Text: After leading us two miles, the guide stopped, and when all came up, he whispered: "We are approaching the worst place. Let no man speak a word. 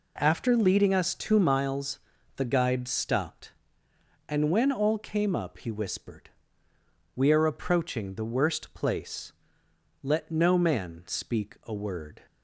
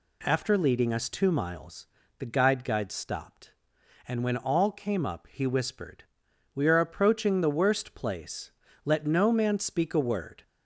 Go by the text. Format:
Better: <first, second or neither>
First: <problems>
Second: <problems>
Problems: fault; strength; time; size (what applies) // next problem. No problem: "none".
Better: first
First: none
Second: says "guide" twice; at 2.6 s